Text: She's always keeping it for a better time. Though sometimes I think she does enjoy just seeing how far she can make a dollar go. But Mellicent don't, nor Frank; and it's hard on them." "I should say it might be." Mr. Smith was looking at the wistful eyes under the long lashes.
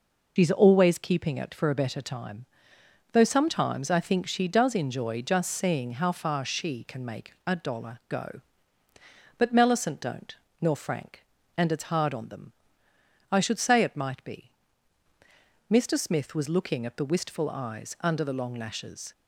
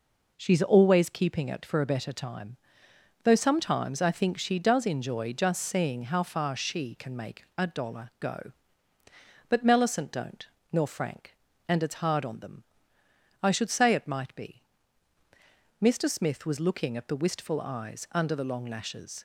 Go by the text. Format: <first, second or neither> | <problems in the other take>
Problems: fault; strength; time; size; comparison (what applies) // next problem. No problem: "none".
second | loses the start of "She's"; at 0.3 s; 100 ms